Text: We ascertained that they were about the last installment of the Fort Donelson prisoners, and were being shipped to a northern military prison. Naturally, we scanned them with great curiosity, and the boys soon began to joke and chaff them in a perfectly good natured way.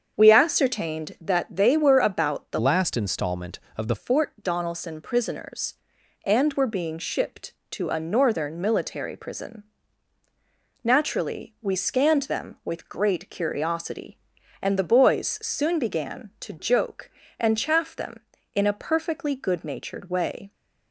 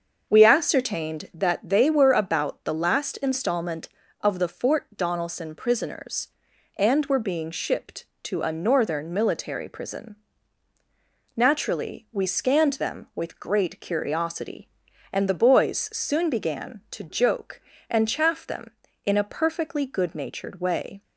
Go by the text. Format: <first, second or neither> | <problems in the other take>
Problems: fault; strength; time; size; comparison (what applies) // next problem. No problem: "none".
second | starts louder than the rest; until 1.1 s; 7 dB; also in the second // changes voice from "last" to "the"; from 2.5 to 3.9 s; 1.4 s long